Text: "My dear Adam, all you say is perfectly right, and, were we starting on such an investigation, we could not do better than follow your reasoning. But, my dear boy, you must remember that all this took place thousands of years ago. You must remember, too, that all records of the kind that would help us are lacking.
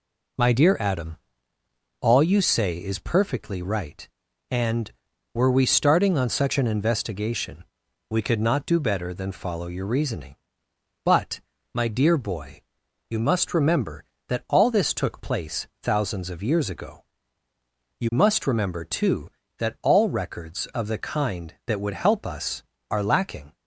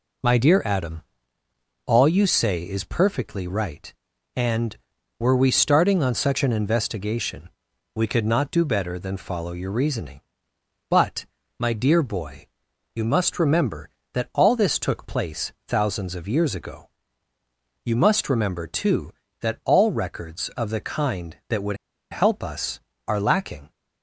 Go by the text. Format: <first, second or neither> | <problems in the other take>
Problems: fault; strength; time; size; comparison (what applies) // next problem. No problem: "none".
first | pauses between "would" and "help"; slight; at 21.7 s; 0.34 s long